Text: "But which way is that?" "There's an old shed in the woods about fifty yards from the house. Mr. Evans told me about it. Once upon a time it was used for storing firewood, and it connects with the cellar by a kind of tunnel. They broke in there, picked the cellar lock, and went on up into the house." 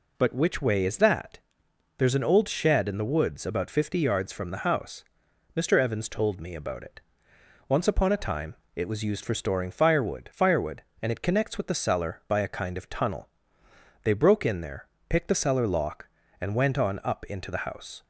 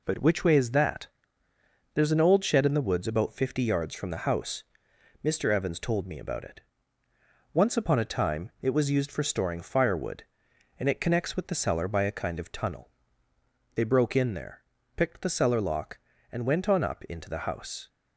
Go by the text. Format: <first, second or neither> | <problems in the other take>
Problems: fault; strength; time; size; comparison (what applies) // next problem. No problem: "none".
second | pauses between "time" and "it"; slight; at 8.5 s; 0.20 s long // says "firewood" twice; at 10.3 s